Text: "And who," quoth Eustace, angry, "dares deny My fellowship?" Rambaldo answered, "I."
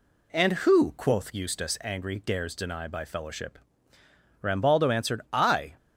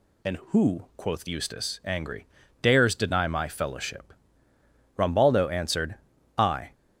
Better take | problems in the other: second | says "By" for "My"; at 2.8 s

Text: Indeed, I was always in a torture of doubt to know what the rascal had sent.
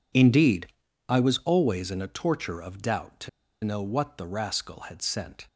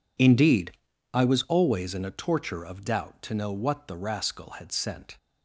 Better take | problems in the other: second | pauses between "to" and "know"; slight; at 3.2 s; 0.35 s long

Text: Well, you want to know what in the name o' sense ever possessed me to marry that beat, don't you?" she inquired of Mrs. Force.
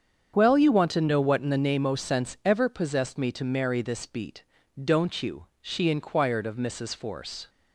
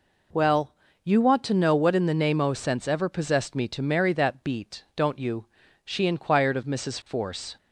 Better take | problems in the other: second | starts louder than the rest; strong; until 1.3 s; 7.5 dB // says "this" for "that"; at 3.8 s

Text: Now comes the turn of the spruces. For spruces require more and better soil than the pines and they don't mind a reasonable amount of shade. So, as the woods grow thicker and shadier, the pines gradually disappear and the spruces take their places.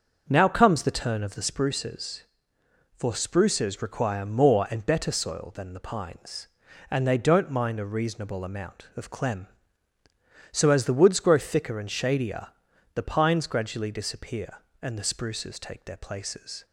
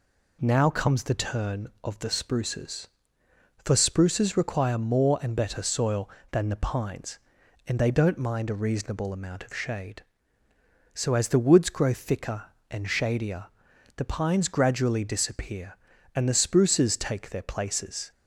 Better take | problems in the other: second | starts louder than the rest; until 1.2 s; 6.5 dB // says "clem" for "shade"; at 9.0 s

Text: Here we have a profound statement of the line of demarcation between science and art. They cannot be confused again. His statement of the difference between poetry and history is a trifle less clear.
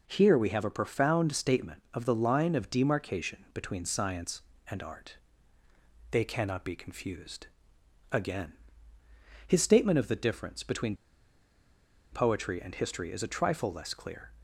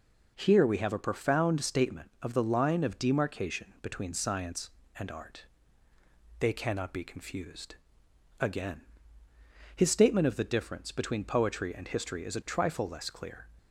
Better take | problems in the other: second | pauses between "confused" and "again"; noticeable; at 7.4 s; 0.64 s long; noticeable in the second // pauses between "between" and "poetry"; at 10.9 s; 1.1 s long

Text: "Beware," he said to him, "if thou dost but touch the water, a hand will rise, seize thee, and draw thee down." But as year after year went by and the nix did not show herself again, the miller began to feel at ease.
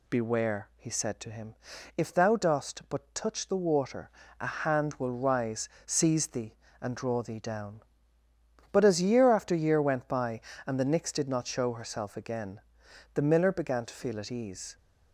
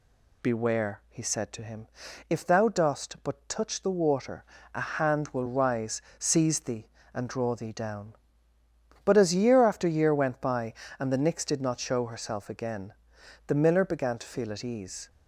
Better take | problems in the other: neither | none

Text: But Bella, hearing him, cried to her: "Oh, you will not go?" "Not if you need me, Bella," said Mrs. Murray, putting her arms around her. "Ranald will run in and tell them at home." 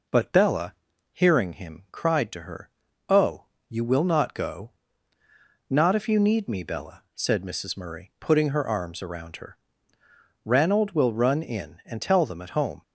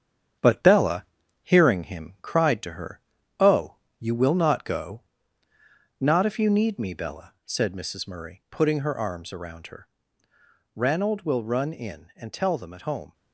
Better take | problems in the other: first | gets quieter; noticeable; throughout; 6 dB

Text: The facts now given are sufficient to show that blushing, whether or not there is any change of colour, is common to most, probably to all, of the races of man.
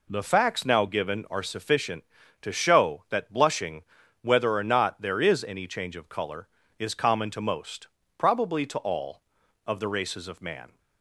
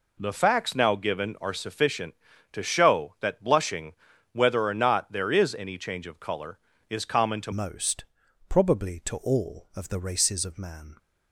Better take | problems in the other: first | changes voice at "most"; from 7.5 s on; 3.4 s long

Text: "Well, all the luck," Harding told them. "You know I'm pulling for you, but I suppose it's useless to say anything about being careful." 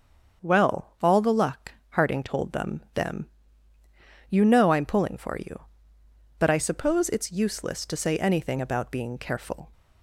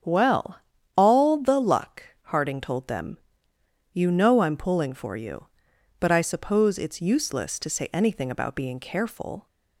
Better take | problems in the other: second | starts louder than the rest; until 1.4 s; 7 dB; strong in the second // says "them" twice; at 2.9 s

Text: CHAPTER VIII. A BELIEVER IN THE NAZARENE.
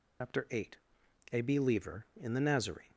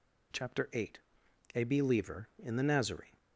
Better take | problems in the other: second | loses the start of "CHAPTER"; at 0.2 s; 115 ms

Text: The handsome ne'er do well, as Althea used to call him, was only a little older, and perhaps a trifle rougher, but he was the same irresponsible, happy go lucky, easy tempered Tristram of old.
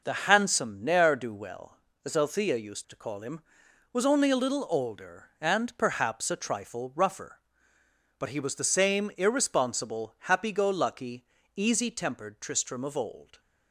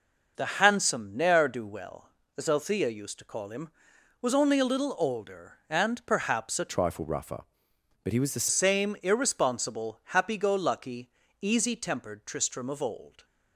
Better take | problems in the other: first | changes voice from "trifle" to "the"; from 6.6 to 8.4 s; 1.8 s long

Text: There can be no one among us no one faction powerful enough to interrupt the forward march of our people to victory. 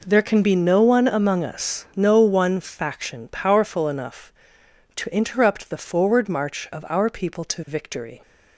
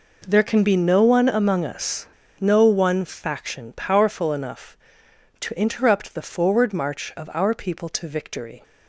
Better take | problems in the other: first | pauses between "us" and "no"; slight; at 2.0 s; 0.31 s long

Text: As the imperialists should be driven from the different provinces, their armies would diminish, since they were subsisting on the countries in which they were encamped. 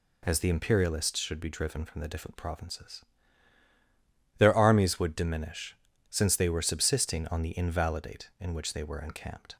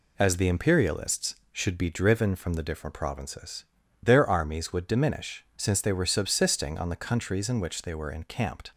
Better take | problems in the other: second | says "invalidate" for "countries"; at 7.5 s

